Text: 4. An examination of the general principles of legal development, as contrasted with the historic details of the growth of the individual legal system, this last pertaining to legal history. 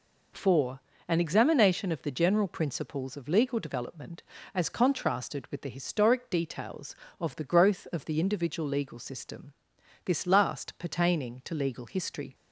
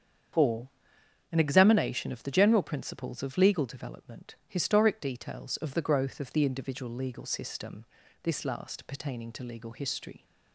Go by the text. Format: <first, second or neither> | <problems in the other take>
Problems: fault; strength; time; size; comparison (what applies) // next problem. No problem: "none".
first | starts louder than the rest; strong; until 1.9 s; 8 dB // skips "as contrasted with the"; at 4.4 s